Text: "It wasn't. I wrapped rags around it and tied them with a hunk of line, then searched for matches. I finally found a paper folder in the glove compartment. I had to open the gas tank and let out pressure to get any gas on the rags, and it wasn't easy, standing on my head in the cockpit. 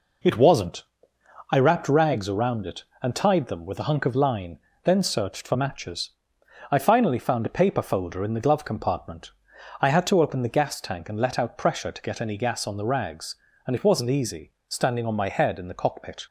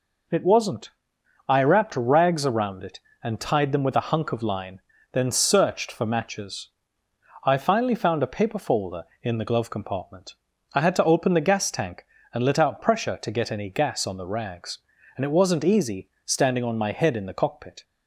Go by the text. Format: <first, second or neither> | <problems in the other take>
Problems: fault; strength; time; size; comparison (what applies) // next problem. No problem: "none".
neither | none